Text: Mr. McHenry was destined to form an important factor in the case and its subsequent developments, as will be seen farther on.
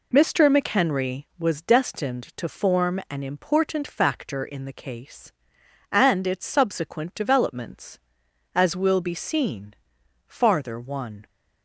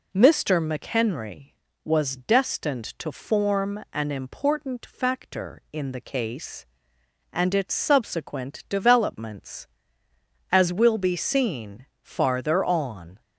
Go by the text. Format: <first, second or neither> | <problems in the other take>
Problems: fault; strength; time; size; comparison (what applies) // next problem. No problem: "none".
second | pauses between "seen" and "farther"; noticeable; at 9.7 s; 0.54 s long; slight in the second // says "one" for "on"; at 10.7 s